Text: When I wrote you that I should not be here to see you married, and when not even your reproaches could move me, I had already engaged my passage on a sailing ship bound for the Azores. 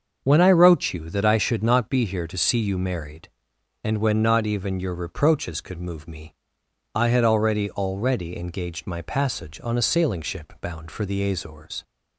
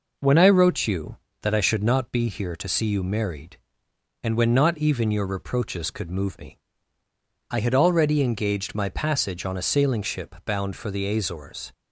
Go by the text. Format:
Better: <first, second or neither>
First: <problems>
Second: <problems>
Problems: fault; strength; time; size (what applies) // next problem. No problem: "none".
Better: second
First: starts louder than the rest; until 1.2 s; 6 dB // says "already" twice; at 7.7 s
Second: none